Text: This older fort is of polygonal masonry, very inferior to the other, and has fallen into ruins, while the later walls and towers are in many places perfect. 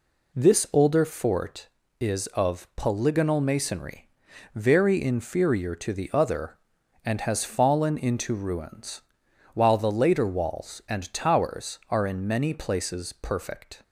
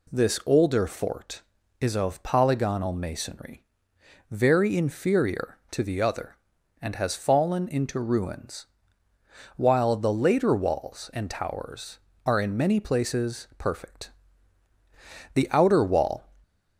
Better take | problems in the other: first | goes on to say "The outer wall"; noticeable; from 15.3 s on; 0.94 s long

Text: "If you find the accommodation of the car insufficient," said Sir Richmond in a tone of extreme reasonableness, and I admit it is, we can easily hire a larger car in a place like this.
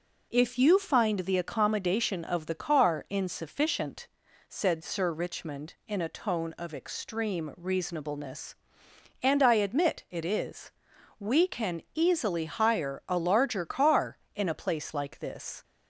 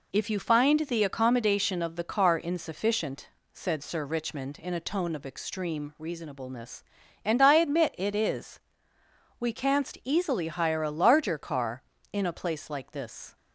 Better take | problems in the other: first | says "canst" for "can"; at 9.5 s

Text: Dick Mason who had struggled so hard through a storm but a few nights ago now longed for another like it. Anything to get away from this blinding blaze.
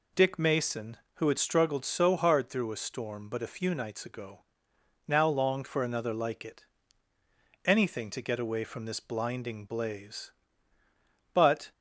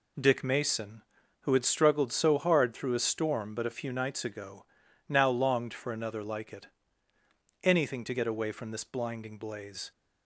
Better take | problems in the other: second | pauses between "ago" and "now"; noticeable; at 4.4 s; 0.66 s long; also in the second // goes on to say "But"; slight; from 11.3 s on; 0.38 s long

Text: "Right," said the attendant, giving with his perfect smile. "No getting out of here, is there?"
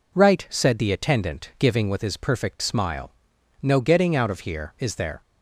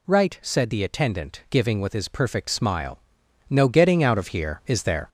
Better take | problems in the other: first | gets louder; slight; throughout; 3.5 dB

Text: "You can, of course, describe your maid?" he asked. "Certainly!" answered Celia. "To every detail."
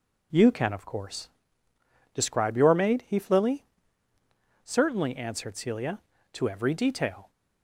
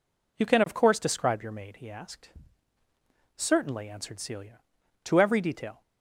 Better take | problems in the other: second | says "flilly" for "asked"; at 3.1 s

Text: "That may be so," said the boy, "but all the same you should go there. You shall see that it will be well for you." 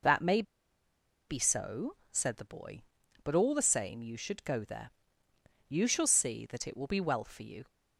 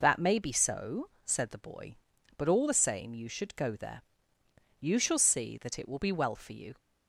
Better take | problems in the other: second | pauses between "may" and "be"; noticeable; at 0.4 s; 0.86 s long

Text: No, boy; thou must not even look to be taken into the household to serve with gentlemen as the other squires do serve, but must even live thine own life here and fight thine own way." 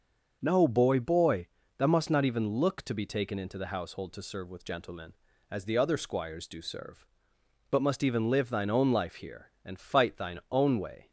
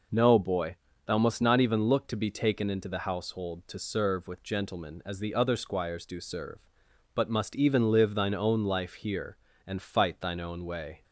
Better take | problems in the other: second | starts louder than the rest; until 1.4 s; 6.5 dB // says "boy" twice; at 1.0 s

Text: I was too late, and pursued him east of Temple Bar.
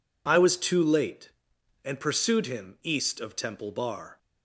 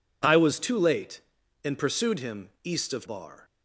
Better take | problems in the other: first | pauses between "him" and "east"; slight; at 2.4 s; 0.16 s long // skips "Temple"; at 3.0 s

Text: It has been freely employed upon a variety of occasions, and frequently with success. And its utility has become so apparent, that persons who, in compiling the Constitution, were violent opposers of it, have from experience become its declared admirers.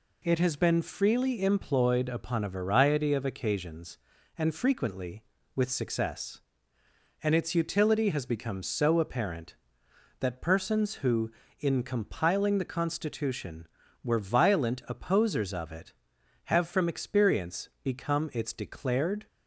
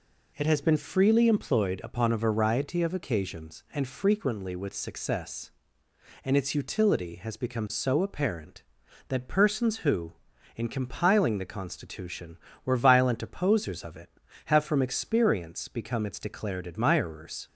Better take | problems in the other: second | stops before "admirers"; at 19.2 s

